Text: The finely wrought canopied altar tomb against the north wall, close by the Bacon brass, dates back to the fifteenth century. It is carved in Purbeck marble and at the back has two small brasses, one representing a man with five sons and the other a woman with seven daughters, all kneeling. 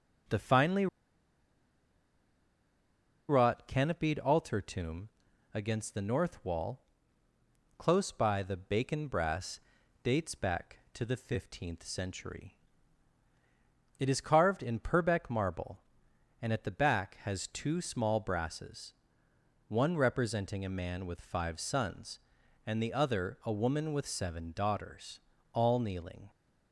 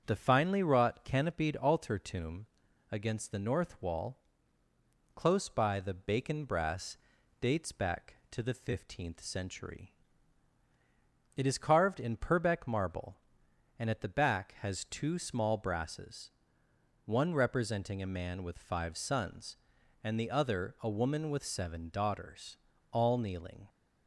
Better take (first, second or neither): second